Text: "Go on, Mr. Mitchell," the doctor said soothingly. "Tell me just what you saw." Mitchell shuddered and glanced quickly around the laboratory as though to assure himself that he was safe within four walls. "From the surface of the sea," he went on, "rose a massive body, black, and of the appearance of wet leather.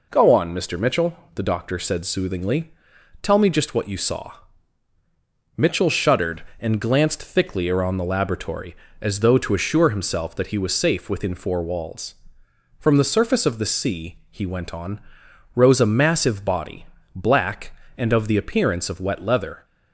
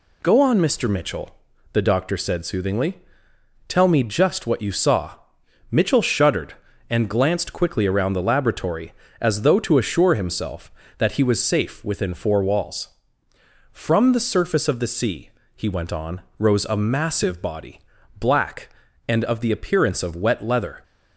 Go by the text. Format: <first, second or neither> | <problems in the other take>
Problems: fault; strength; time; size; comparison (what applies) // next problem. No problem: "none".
second | says "thickly" for "quickly"; at 7.2 s